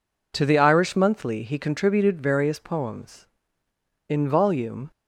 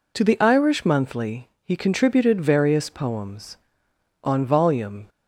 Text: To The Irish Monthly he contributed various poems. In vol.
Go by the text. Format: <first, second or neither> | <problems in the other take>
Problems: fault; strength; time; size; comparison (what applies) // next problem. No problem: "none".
first | says "On" for "In"; at 4.2 s